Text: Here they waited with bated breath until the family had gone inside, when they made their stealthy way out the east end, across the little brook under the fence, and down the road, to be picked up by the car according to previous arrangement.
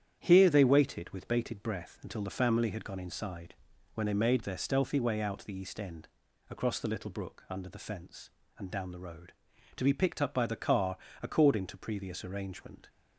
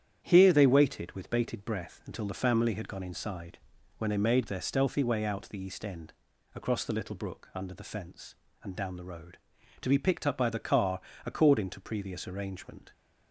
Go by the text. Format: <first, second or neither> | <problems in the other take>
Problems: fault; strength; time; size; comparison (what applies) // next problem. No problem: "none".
neither | starts louder than the rest; strong; the same in both // pauses between "car" and "according"; slight; the same in both